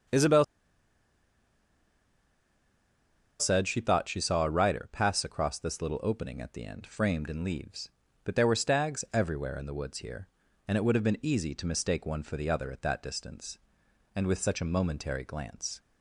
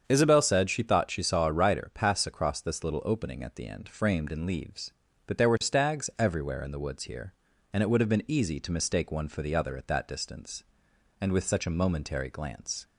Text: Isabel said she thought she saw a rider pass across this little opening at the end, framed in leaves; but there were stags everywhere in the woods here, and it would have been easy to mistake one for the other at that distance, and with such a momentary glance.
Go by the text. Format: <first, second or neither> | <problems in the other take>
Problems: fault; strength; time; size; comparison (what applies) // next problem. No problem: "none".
second | starts louder than the rest; strong; until 4.0 s; 7.5 dB; strong in the second // pauses between "Isabel" and "said"; strong; at 0.4 s; 2.9 s long